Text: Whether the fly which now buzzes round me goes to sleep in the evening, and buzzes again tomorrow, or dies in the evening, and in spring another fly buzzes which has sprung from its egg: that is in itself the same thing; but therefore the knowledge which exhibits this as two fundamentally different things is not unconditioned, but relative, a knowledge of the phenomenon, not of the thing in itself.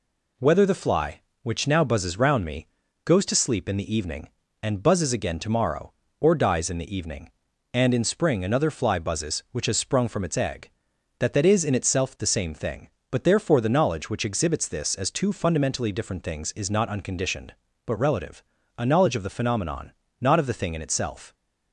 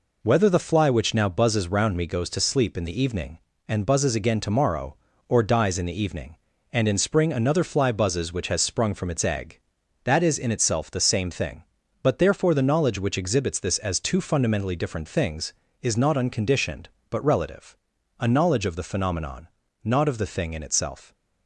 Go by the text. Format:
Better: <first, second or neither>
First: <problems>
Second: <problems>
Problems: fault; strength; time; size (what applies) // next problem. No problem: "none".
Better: second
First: pauses between "me" and "goes"; at 2.6 s; 0.38 s long // says "that" twice; at 11.3 s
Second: none